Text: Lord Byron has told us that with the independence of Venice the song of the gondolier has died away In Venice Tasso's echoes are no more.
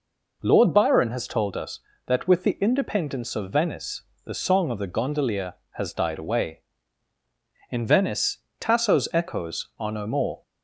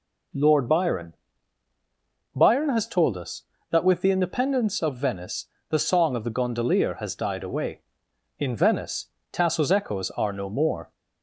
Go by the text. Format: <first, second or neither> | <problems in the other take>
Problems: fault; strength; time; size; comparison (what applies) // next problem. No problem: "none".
first | says "Byron" twice; at 2.3 s // pauses between "Venice" and "the"; slight; at 5.4 s; 0.24 s long; slight in the first // pauses between "Venice" and "Tasso's"; slight; at 9.0 s; 0.26 s long; slight in the first